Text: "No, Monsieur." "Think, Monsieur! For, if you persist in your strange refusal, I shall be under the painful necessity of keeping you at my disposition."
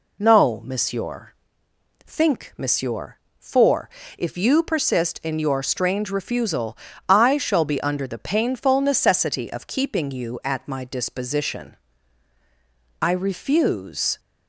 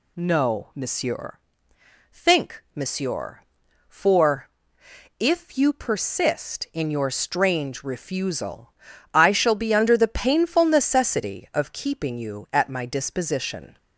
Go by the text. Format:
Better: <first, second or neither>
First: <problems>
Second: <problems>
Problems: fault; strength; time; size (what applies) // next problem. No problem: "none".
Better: second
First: goes on to say "I refuse"; noticeable; from 13.0 s on; 1.1 s long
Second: none